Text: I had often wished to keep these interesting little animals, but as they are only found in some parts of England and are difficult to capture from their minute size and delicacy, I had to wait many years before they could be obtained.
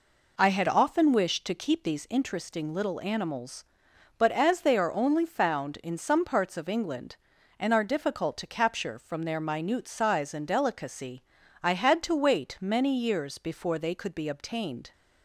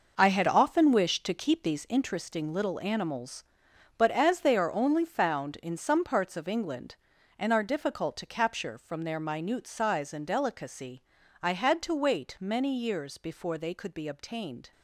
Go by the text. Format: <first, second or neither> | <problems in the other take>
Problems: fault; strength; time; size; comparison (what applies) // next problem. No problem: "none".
first | gets quieter; strong; throughout; 10 dB